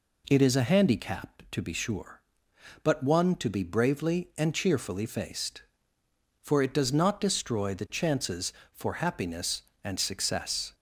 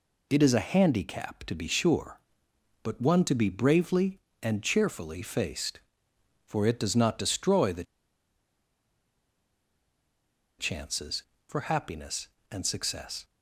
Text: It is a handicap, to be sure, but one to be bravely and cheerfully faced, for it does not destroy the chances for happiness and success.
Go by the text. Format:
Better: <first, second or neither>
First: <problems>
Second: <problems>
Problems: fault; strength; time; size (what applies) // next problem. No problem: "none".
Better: first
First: none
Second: pauses between "the" and "chances"; strong; at 7.8 s; 2.7 s long